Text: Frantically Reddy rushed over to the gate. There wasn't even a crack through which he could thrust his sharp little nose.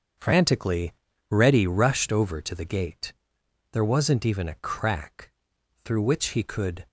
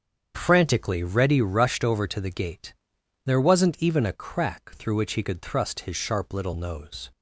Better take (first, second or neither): second